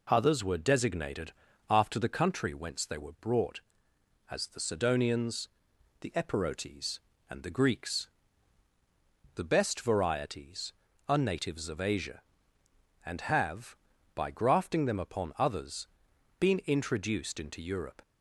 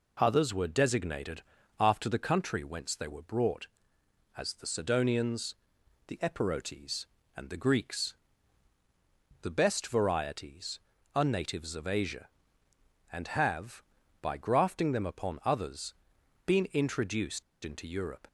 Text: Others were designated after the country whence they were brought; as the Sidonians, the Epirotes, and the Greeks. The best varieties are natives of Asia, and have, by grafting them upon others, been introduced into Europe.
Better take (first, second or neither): first